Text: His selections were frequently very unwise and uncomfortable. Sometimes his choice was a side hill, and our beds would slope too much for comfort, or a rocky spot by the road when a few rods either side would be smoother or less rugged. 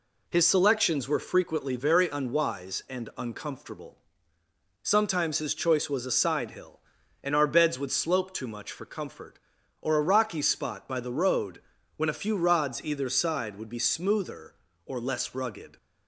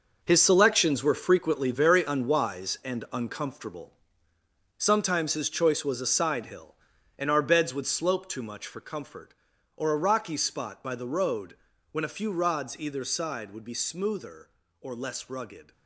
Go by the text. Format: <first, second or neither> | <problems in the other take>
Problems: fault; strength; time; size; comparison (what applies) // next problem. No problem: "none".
first | gets quieter; strong; throughout; 11 dB // pauses between "road" and "when"; slight; at 11.5 s; 0.34 s long; slight in the first